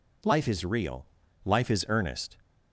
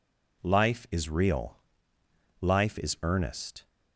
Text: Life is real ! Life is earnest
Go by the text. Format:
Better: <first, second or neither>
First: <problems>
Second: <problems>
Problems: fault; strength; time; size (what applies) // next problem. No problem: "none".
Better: neither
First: none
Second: none